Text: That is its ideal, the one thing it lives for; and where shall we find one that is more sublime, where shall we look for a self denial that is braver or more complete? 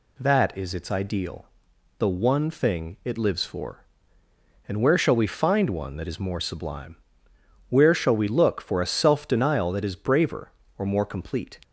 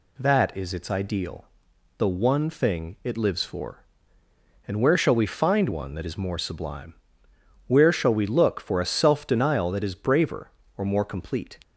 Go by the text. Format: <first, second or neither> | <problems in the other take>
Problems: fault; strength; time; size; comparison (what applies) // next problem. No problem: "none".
neither | none